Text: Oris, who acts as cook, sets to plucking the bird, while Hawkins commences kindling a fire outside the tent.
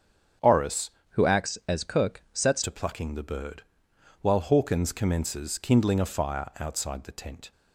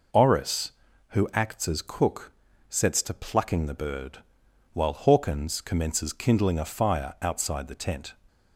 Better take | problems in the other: second | starts louder than the rest; strong; until 1.7 s; 7.5 dB // changes voice from "who" to "sets"; from 1.1 to 2.6 s; 1.5 s long

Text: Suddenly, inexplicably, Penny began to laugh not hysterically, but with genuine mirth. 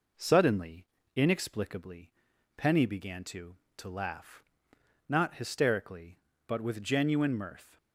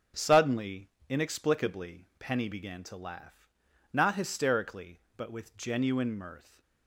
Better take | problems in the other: second | says "to" twice; at 3.7 s // pauses between "laugh" and "not"; noticeable; at 4.4 s; 0.66 s long; also in the second

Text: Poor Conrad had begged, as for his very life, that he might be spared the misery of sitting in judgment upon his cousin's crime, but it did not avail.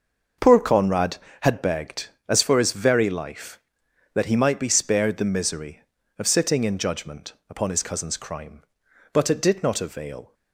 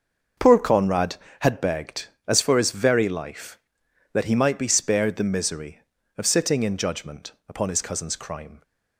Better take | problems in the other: first | starts louder than the rest; noticeable; until 1.6 s; 6 dB; noticeable in the first // pauses between "judgment" and "upon"; slight; at 7.3 s; 0.16 s long; slight in the first // stops before "but it did not avail"; at 8.6 s

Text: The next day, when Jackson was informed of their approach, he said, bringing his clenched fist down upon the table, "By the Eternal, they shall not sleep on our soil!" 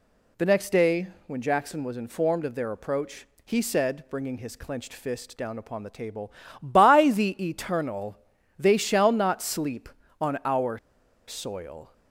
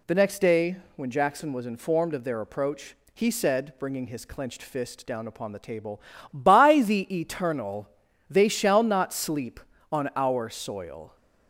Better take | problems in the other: second | pauses between "our" and "soil"; noticeable; at 10.7 s; 0.51 s long

